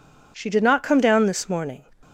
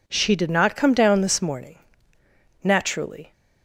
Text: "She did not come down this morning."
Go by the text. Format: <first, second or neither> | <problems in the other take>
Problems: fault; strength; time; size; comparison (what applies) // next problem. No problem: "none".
first | goes on to say "Naturally"; noticeable; from 2.6 s on; 0.70 s long